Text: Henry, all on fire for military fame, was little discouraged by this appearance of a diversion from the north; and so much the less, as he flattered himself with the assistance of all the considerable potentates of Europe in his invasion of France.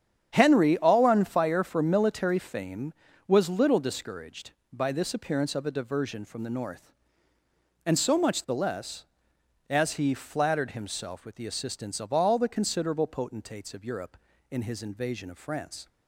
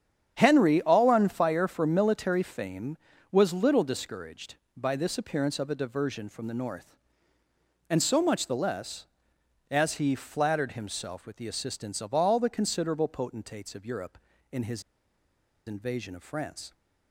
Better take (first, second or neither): first